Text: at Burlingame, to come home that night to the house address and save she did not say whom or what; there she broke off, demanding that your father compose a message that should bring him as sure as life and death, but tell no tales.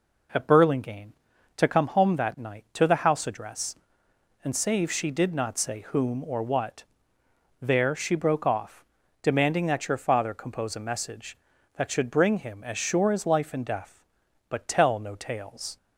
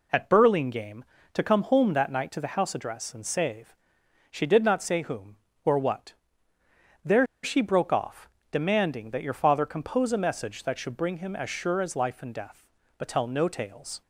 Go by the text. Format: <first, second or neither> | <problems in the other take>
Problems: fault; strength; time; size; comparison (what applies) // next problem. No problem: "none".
first | pauses between "save" and "she"; noticeable; at 3.7 s; 0.56 s long // pauses between "there" and "she"; slight; at 7.2 s; 0.18 s long